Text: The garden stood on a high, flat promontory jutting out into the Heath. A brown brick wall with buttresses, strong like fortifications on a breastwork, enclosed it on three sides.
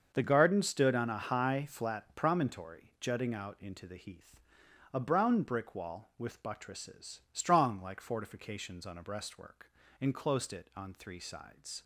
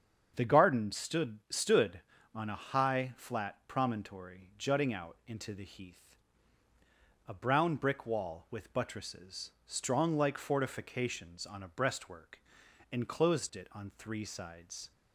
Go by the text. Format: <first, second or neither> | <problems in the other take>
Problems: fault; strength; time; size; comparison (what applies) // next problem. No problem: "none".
first | starts louder than the rest; strong; until 1.3 s; 7.5 dB; also in the first // says "stood" twice; at 1.4 s